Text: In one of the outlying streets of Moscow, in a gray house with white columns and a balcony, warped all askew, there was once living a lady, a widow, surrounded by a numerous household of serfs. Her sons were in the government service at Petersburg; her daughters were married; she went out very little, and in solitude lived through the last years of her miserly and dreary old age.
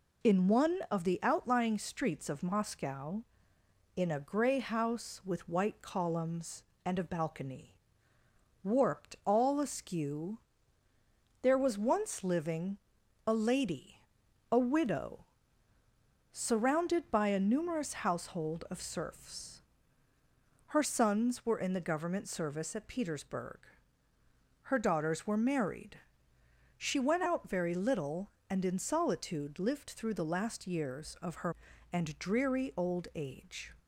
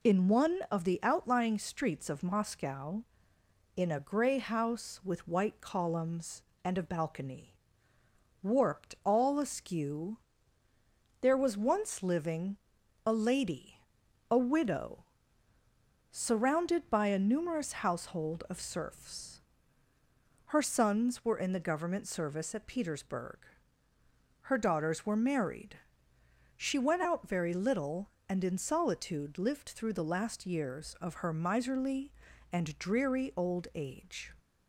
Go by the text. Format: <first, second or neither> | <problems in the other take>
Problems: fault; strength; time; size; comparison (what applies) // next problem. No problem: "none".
second | pauses between "living" and "a"; noticeable; at 12.7 s; 0.48 s long; noticeable in the second // skips "miserly"; at 31.7 s